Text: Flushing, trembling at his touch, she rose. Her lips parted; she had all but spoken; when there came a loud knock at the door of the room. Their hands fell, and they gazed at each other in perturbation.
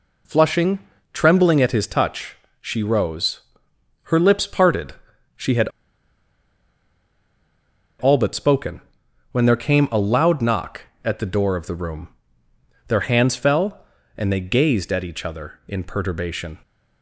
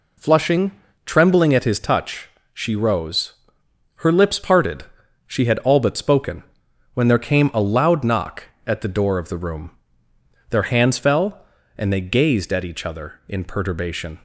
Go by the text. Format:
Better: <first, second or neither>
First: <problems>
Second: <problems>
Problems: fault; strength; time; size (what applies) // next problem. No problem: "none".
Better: second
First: pauses between "had" and "all"; strong; at 5.6 s; 2.3 s long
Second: none